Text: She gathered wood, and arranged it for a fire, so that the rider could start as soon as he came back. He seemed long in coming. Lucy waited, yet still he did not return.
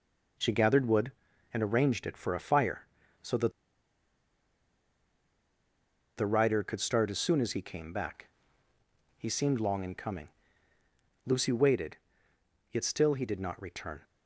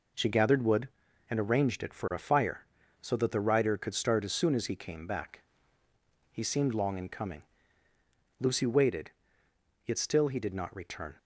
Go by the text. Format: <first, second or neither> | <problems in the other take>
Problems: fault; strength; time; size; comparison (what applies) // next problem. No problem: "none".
second | pauses between "that" and "the"; strong; at 3.5 s; 2.6 s long